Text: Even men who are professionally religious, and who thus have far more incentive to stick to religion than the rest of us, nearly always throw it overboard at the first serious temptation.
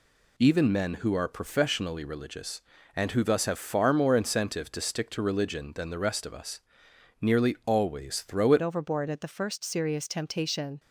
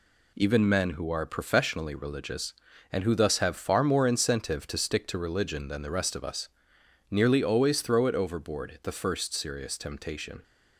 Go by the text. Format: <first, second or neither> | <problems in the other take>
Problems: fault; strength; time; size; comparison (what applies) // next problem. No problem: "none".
second | changes voice at "overboard"; from 8.6 s on; 2.1 s long